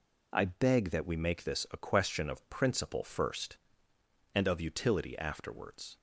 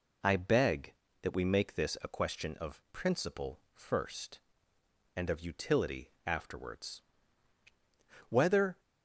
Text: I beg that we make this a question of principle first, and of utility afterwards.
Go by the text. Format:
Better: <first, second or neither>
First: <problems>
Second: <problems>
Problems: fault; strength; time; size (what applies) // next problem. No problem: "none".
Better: first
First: none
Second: pauses between "utility" and "afterwards"; slight; at 6.0 s; 0.16 s long // goes on to say "Whether"; from 8.2 s on; 0.50 s long